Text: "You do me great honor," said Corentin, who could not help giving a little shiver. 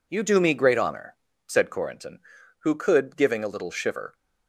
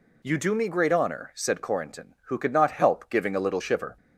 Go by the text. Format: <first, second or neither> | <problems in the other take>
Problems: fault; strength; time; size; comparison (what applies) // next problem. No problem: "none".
second | skips "not help"; at 3.1 s